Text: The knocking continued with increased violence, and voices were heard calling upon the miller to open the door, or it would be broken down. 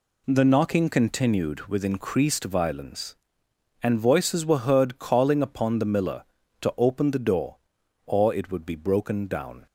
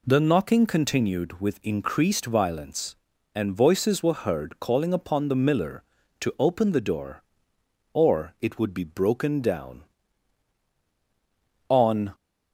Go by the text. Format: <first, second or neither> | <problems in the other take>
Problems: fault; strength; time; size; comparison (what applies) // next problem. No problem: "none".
first | goes on to say "On"; slight; from 11.7 s on; 0.44 s long